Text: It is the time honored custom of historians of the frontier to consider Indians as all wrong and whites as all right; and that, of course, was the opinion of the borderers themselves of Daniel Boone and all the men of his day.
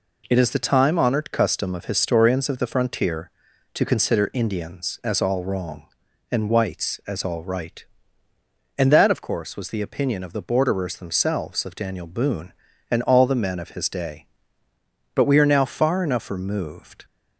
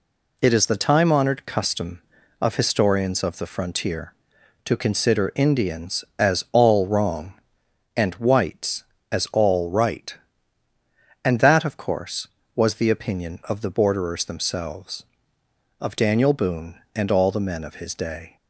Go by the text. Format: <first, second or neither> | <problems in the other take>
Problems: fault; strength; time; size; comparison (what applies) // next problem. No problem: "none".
second | goes on to say "But we are now far enough removed"; strong; from 15.1 s on; 1.9 s long